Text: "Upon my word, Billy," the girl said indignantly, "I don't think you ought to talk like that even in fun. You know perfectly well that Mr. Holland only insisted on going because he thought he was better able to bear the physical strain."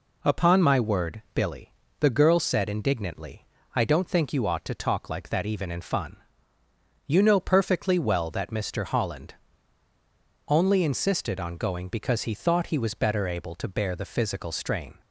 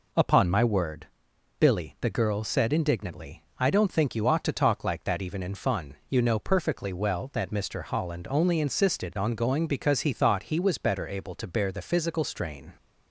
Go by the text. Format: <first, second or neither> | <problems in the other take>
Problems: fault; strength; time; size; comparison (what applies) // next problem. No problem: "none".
second | pauses between "Holland" and "only"; at 9.3 s; 1.1 s long